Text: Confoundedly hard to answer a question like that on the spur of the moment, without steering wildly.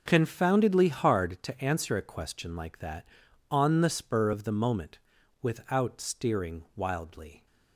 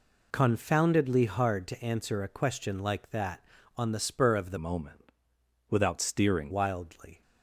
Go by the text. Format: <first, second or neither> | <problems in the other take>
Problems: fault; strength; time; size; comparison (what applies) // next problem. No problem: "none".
first | changes voice from "moment" to "steering"; from 4.5 to 6.5 s; 2.0 s long